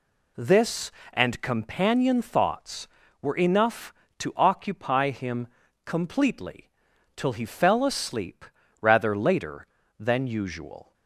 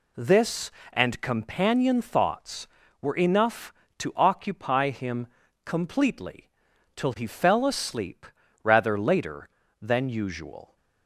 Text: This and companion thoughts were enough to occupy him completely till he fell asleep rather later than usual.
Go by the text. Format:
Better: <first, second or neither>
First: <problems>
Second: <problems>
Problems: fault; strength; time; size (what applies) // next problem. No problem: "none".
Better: neither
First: pauses between "him" and "completely"; at 5.4 s; 0.38 s long // pauses between "completely" and "till"; noticeable; at 6.7 s; 0.46 s long // pauses between "asleep" and "rather"; slight; at 8.4 s; 0.35 s long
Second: pauses between "him" and "completely"; at 5.2 s; 0.38 s long // pauses between "completely" and "till"; noticeable; at 6.4 s; 0.46 s long // pauses between "asleep" and "rather"; slight; at 8.2 s; 0.36 s long